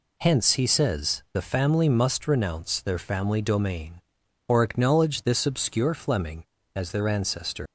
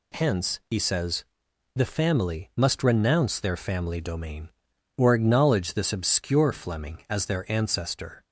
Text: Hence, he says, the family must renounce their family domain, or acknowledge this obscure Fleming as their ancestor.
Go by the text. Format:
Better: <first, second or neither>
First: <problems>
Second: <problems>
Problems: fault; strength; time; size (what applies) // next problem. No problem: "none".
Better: second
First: leaves "ancestor" unfinished; at 7.6 s; 95 ms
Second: none